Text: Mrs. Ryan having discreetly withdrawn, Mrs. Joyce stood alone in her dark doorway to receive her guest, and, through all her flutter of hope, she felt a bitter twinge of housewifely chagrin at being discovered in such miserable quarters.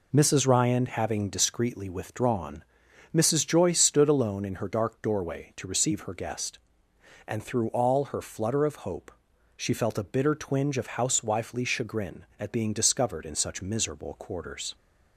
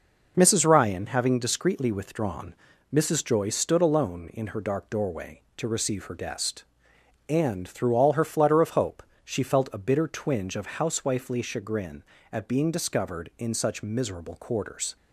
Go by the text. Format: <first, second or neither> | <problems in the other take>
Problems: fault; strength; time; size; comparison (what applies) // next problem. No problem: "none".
neither | none